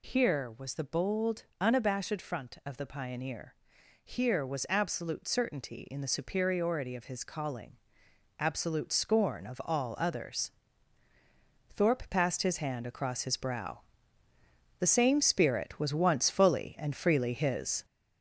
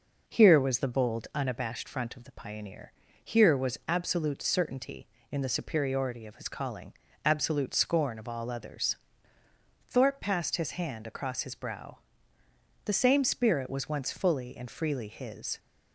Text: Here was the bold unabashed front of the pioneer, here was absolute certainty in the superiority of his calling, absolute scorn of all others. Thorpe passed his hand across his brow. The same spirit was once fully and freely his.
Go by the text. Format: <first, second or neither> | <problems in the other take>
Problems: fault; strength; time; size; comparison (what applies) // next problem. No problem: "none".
second | gets louder; noticeable; throughout; 5.5 dB